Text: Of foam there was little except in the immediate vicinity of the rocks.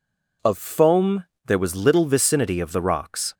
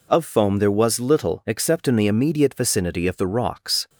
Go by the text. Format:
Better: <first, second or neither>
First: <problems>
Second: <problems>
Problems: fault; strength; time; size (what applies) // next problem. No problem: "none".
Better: second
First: pauses between "foam" and "there"; slight; at 1.2 s; 0.18 s long // skips "except in the immediate"; at 2.0 s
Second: none